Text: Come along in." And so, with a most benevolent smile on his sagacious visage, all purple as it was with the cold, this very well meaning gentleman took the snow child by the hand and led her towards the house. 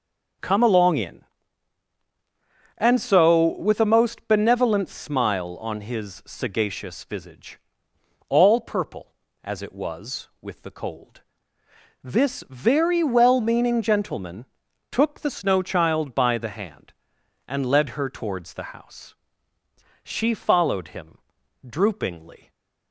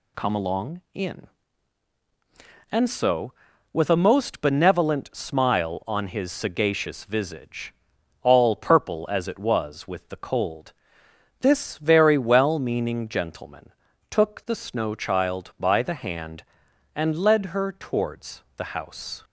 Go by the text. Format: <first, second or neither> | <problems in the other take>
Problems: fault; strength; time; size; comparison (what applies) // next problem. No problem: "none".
second | starts louder than the rest; noticeable; until 2.9 s; 6 dB // pauses between "gentleman" and "took"; at 14.4 s; 0.44 s long; also in the second // goes on to say "She followed him droopingly"; strong; from 19.7 s on; 2.7 s long